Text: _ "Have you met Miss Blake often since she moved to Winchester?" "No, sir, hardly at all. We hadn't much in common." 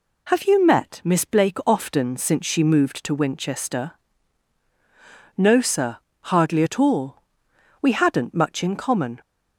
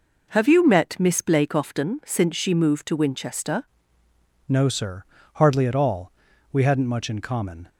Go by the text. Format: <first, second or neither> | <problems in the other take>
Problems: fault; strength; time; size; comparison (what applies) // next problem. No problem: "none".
first | changes voice at "No"; from 4.4 s on; 3.2 s long